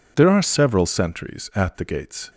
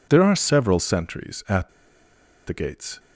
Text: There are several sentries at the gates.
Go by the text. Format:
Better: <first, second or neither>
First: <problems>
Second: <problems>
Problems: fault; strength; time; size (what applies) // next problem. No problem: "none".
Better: first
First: none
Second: pauses between "at" and "the"; noticeable; at 1.6 s; 0.79 s long